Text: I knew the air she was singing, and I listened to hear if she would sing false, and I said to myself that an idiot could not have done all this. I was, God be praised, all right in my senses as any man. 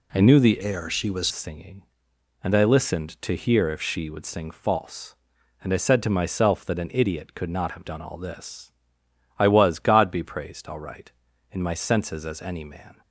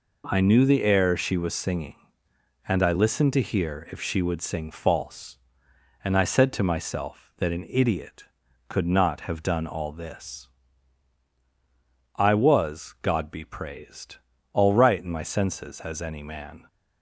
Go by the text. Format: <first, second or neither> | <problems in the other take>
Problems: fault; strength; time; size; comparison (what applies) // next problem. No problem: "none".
second | changes voice from "air" to "was"; from 0.6 to 1.2 s; 0.6 s long